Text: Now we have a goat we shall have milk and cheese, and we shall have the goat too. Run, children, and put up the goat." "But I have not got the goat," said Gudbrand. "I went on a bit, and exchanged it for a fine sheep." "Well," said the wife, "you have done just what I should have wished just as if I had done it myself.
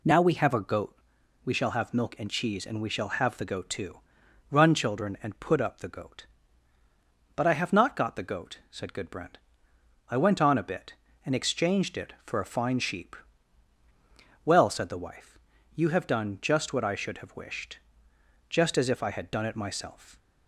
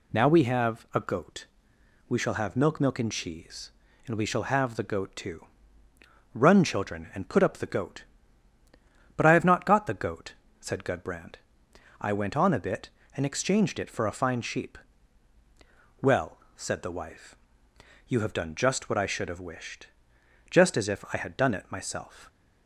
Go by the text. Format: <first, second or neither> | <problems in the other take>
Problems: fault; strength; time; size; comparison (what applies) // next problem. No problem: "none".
first | pauses between "goat" and "we"; noticeable; at 1.4 s; 0.64 s long; noticeable in the first // says "milk" twice; at 2.8 s // pauses between "wished" and "just"; noticeable; at 19.8 s; 0.62 s long; noticeable in the first